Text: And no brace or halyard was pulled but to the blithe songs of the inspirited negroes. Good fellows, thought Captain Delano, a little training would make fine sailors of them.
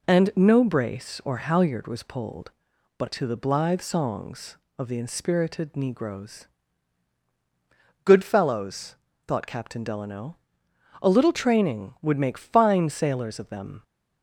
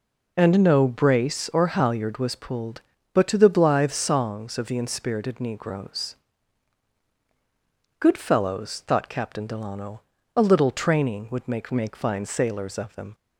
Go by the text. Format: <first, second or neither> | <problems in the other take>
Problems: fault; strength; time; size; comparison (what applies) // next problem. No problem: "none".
first | says "make" twice; at 11.7 s